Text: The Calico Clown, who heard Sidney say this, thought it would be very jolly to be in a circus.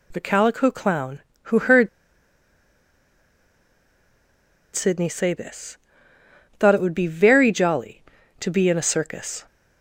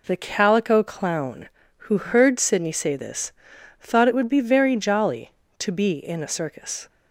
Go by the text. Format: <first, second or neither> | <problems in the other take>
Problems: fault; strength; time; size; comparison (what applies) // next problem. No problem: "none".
second | pauses between "heard" and "Sidney"; strong; at 1.8 s; 2.8 s long